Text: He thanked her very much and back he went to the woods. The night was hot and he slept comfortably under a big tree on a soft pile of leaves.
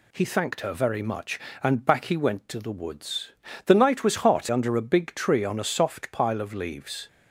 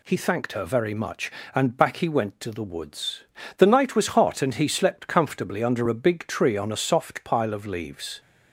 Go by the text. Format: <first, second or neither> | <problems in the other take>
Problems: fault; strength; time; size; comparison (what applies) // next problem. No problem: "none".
second | skips "and he slept comfortably"; at 4.4 s